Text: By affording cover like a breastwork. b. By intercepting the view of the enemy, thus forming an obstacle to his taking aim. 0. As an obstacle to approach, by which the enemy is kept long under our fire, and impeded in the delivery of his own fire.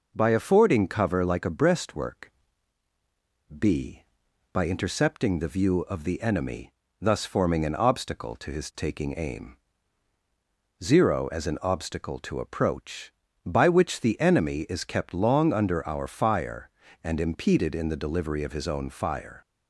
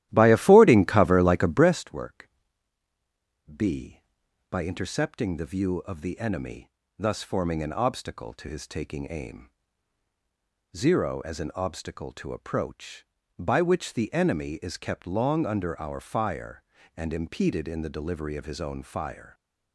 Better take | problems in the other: first | starts louder than the rest; strong; until 1.9 s; 13.5 dB

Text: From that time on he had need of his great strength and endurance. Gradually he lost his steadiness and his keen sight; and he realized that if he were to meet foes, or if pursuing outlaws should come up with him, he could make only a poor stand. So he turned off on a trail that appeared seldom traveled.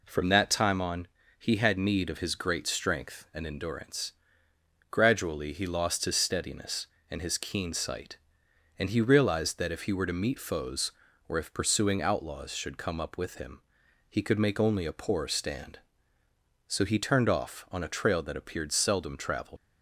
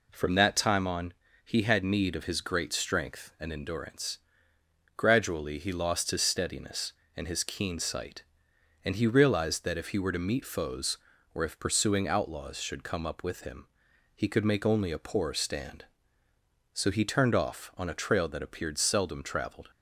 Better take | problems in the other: second | pauses between "on" and "he"; slight; at 1.0 s; 0.32 s long; slight in the second // leaves "traveled" unfinished; at 19.5 s; 75 ms

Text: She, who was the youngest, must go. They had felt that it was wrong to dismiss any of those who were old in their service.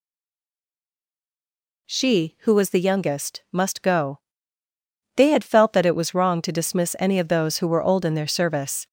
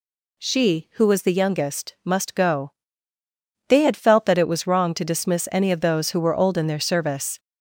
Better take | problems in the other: second | stays silent before the first word; noticeable; until 1.8 s; 1.8 s long

